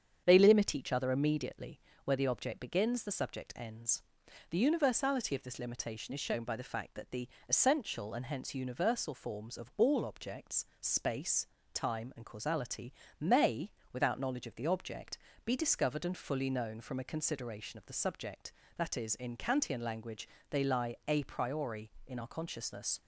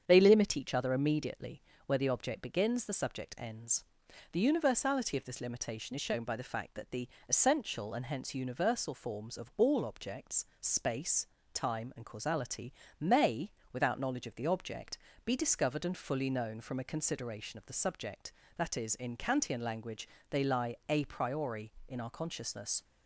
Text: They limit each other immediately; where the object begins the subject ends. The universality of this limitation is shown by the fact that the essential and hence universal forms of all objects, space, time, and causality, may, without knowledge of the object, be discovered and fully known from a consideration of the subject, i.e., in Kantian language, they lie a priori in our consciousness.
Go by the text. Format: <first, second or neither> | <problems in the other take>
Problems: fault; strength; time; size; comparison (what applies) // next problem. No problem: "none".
neither | starts louder than the rest; strong; the same in both // pauses between "the" and "essential"; slight; the same in both